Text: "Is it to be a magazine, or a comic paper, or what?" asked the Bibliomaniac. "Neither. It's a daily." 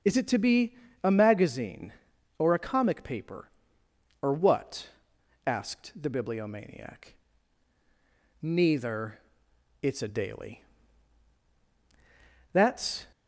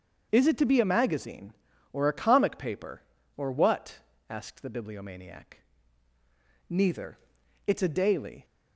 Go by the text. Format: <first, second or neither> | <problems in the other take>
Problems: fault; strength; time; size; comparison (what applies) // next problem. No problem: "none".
second | starts louder than the rest; until 1.3 s; 6.5 dB; also in the second // pauses between "be" and "a"; slight; at 0.7 s; 0.30 s long // goes on to say "That's"; from 12.5 s on; 0.56 s long